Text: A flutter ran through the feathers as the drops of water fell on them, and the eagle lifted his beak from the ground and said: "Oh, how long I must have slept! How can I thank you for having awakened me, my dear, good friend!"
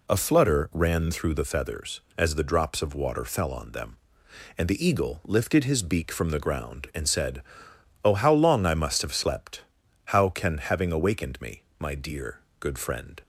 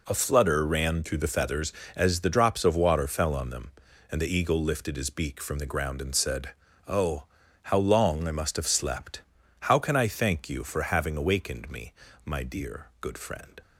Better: second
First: skips "I thank you for"; at 10.5 s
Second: none

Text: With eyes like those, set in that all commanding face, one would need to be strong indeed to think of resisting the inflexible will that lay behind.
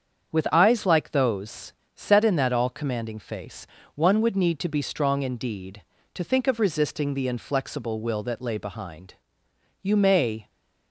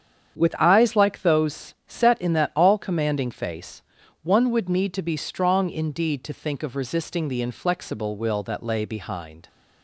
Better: second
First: starts louder than the rest; strong; until 1.3 s; 7.5 dB // goes on to say "You may"; noticeable; from 9.8 s on; 0.68 s long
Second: starts louder than the rest; strong; until 1.4 s; 8 dB

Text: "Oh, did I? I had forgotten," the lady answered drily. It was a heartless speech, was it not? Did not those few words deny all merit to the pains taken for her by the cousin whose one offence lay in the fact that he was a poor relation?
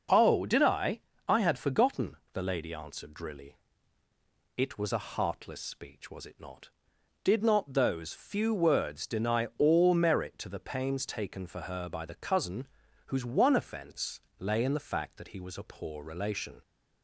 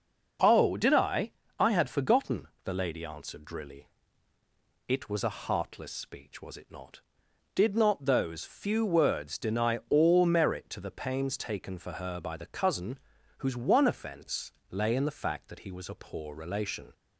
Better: neither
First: pauses between "cousin" and "whose"; at 12.6 s; 0.40 s long // pauses between "offence" and "lay"; slight; at 14.2 s; 0.18 s long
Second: pauses between "cousin" and "whose"; at 12.9 s; 0.40 s long // pauses between "offence" and "lay"; slight; at 14.5 s; 0.18 s long

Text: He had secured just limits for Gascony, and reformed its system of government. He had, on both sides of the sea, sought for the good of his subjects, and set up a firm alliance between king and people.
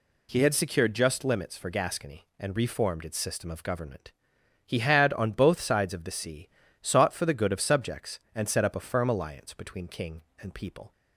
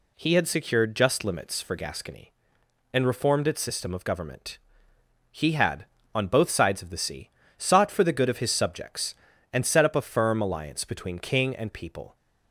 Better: second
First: skips "his"; at 7.5 s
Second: none

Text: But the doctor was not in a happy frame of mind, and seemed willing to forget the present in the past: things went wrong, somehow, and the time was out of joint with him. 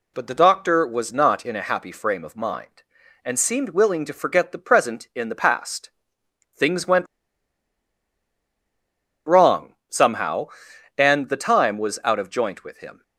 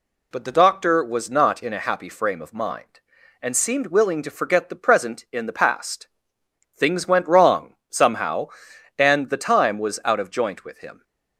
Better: second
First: pauses between "went" and "wrong"; strong; at 7.0 s; 2.2 s long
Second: none

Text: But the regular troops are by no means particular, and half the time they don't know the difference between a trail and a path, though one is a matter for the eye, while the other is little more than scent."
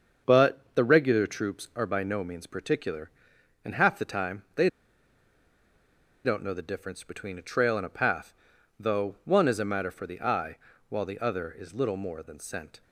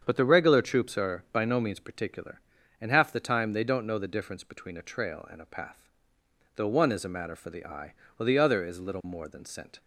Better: second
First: starts louder than the rest; until 1.4 s; 7 dB // pauses between "they" and "don't"; strong; at 4.6 s; 1.5 s long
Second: starts louder than the rest; strong; until 1.0 s; 7.5 dB

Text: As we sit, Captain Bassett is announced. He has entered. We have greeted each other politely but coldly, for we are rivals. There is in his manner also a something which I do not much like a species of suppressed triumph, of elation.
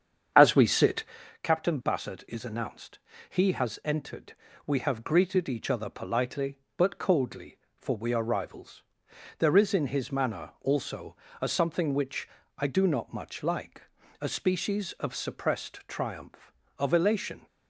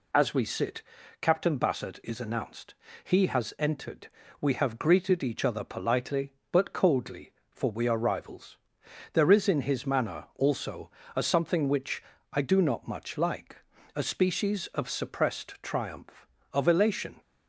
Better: second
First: starts louder than the rest; strong; until 1.3 s; 8 dB // pauses between "also" and "a"; slight; at 11.1 s; 0.24 s long // pauses between "which" and "I"; slight; at 12.2 s; 0.30 s long // pauses between "like" and "a"; at 13.8 s; 0.40 s long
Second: pauses between "also" and "a"; slight; at 10.9 s; 0.24 s long // pauses between "which" and "I"; slight; at 12.0 s; 0.30 s long // pauses between "like" and "a"; at 13.5 s; 0.40 s long

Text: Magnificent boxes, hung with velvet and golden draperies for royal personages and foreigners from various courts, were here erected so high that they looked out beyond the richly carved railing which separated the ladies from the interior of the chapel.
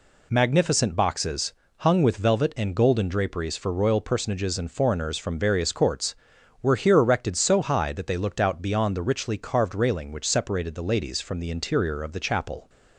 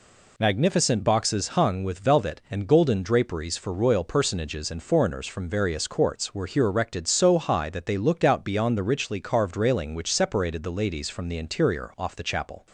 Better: first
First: none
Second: says "off" for "of"; at 11.9 s

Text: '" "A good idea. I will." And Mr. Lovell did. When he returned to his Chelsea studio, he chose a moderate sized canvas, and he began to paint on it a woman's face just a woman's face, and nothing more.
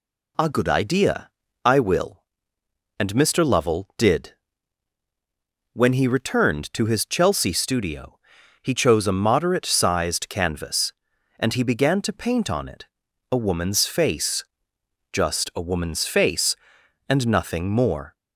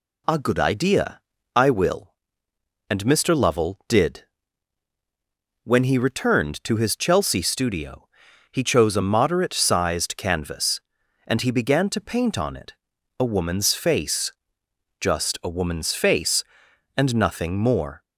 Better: neither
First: pauses between "it" and "a"; at 12.8 s; 0.44 s long // pauses between "face" and "just"; noticeable; at 14.4 s; 0.68 s long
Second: pauses between "it" and "a"; at 12.7 s; 0.44 s long // pauses between "face" and "just"; noticeable; at 14.3 s; 0.68 s long

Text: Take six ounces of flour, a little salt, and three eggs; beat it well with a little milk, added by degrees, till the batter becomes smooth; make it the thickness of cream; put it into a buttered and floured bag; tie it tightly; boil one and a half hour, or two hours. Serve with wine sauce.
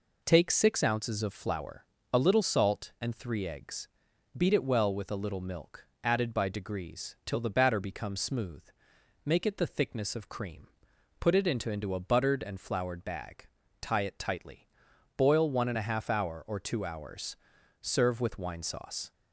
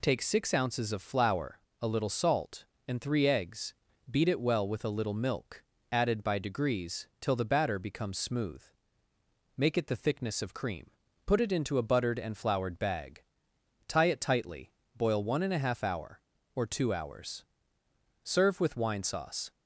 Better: second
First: says "into" twice; at 11.7 s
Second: none

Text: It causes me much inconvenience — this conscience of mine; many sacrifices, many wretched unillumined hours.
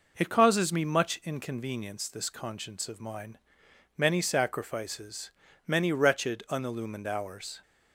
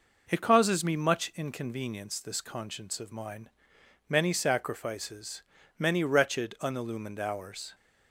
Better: neither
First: none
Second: none

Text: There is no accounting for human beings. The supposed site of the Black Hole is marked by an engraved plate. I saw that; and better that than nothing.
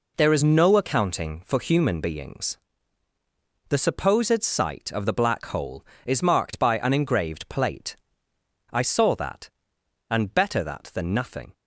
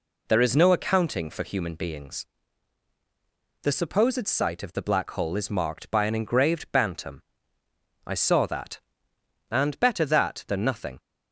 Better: first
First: none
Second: says "bantam" for "plate"; at 6.7 s

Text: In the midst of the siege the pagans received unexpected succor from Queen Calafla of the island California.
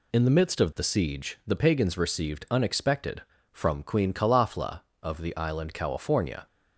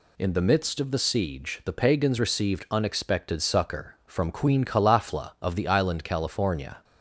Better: second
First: skips "succor"; at 3.3 s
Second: none

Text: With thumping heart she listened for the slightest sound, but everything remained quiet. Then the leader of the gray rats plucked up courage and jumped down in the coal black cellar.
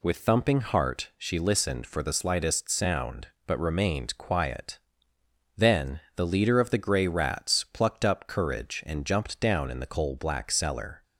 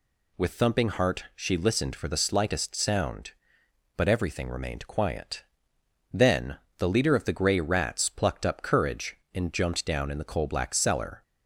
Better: second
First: skips "everything"; at 3.5 s // pauses between "Then" and "the"; slight; at 5.9 s; 0.16 s long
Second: pauses between "Then" and "the"; slight; at 6.5 s; 0.20 s long

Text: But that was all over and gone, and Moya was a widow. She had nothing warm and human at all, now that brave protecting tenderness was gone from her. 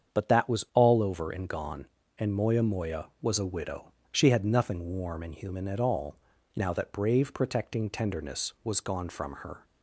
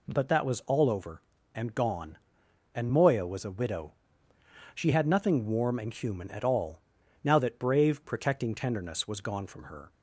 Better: second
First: starts louder than the rest; strong; until 1.2 s; 7.5 dB // says "Moya" twice; at 2.6 s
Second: none

